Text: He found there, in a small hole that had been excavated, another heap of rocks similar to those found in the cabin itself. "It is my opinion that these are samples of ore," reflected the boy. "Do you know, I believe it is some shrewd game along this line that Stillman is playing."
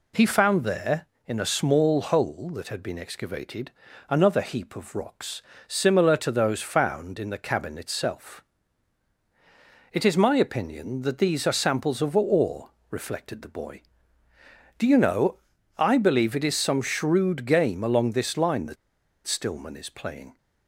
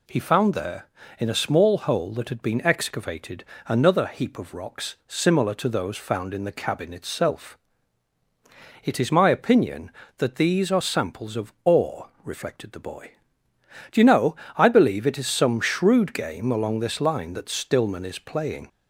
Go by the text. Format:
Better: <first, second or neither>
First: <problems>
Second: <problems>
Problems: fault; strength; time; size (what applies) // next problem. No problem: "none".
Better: second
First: pauses between "rocks" and "similar"; slight; at 5.4 s; 0.24 s long // pauses between "that" and "Stillman"; noticeable; at 18.7 s; 0.51 s long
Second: none